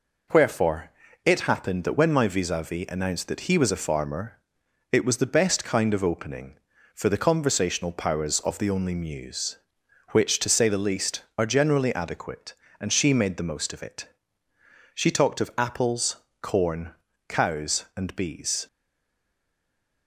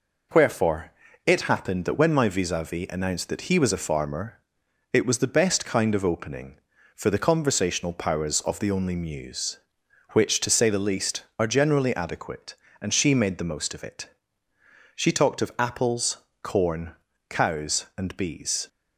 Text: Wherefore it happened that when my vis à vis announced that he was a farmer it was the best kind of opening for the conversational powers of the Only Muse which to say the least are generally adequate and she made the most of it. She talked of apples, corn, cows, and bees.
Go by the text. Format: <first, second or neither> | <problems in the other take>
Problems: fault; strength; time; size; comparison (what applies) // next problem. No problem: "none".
second | pauses between "Wherefore" and "it"; slight; at 0.9 s; 0.34 s long; slight in the second // pauses between "farmer" and "it"; noticeable; at 4.3 s; 0.52 s long; noticeable in the second // stays silent after the last word; noticeable; from 18.6 s on; 1.4 s long